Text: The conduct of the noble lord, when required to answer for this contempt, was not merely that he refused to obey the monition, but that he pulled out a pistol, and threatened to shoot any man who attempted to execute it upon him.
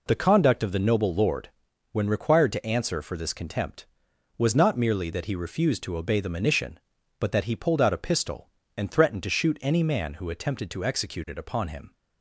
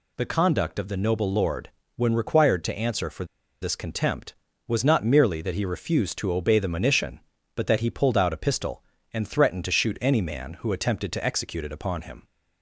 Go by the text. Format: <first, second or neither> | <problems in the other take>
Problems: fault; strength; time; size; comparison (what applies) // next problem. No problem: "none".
first | pauses between "for" and "this"; at 3.2 s; 0.37 s long